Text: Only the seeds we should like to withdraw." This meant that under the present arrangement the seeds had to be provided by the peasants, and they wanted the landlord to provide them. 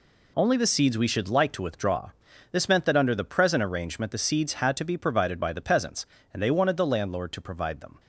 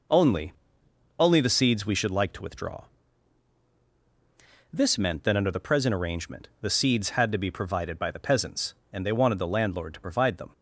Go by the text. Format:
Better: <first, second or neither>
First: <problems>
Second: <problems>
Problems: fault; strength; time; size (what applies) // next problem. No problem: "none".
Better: first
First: none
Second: says "Only" twice; at 1.1 s